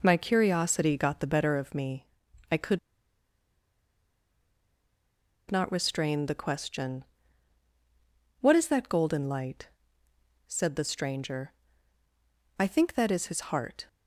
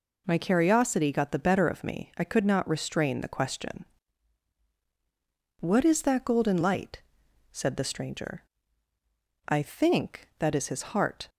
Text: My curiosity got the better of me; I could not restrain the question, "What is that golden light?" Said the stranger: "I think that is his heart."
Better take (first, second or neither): second